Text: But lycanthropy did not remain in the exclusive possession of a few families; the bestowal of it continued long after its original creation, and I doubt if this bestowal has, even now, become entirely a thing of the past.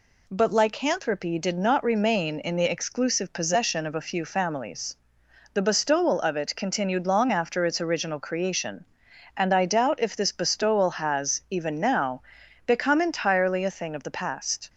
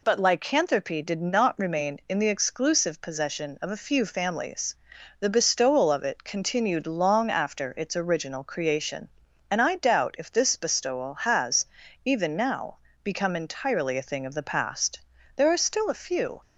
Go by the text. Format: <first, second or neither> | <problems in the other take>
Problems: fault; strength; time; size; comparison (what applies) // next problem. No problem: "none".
first | goes on to say "There are still a few"; noticeable; from 15.3 s on; 1.0 s long